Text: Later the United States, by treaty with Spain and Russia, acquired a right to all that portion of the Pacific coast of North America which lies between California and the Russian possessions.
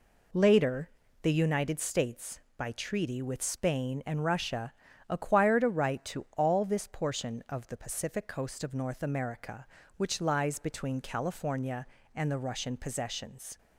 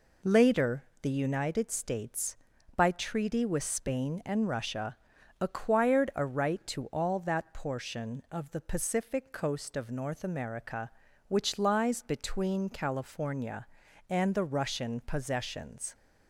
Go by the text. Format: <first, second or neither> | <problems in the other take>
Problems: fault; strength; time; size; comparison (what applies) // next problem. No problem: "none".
second | pauses between "Later" and "the"; slight; at 0.8 s; 0.34 s long; slight in the second // says "this" for "that"; at 6.6 s